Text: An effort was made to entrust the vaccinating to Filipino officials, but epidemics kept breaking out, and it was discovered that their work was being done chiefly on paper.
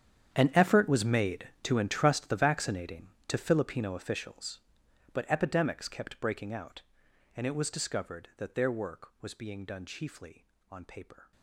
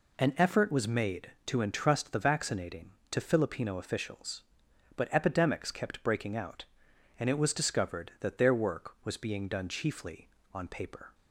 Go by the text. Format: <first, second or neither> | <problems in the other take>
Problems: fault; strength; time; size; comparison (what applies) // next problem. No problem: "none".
second | gets quieter; strong; throughout; 18 dB